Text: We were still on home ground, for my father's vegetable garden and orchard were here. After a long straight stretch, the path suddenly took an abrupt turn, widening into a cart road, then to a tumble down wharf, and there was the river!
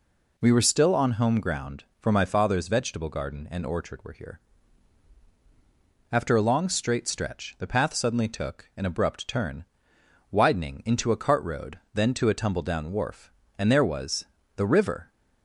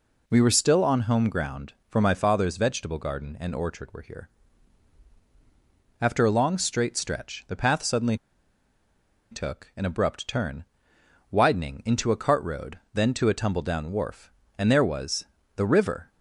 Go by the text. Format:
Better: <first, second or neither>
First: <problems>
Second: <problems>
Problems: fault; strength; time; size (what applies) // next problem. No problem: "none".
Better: first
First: pauses between "was" and "the"; slight; at 14.2 s; 0.30 s long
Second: pauses between "suddenly" and "took"; at 8.1 s; 1.1 s long // pauses between "was" and "the"; slight; at 15.2 s; 0.30 s long